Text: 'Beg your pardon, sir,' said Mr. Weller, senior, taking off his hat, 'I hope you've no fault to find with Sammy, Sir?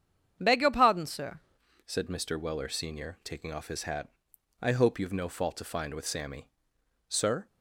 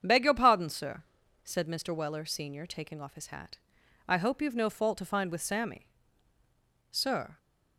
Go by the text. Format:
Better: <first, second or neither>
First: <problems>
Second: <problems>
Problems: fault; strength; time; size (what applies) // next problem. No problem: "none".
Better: second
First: starts louder than the rest; strong; until 1.4 s; 8 dB // changes voice at "said"; from 1.8 s on; 5.6 s long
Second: starts louder than the rest; strong; until 1.0 s; 7.5 dB